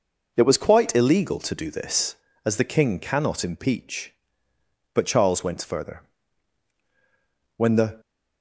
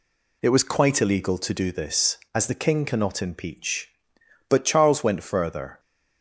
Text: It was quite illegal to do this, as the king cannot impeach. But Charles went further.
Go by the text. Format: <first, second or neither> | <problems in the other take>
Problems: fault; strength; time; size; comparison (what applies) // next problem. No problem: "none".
second | goes on to say "When the"; slight; from 7.5 s on; 0.44 s long